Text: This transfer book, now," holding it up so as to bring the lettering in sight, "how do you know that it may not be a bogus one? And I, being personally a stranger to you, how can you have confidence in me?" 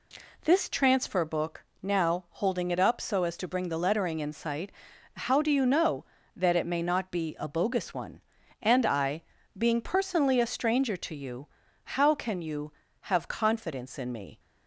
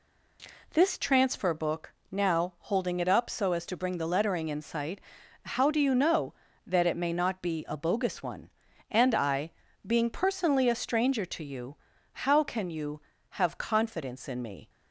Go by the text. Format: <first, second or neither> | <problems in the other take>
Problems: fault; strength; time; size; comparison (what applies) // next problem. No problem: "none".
neither | none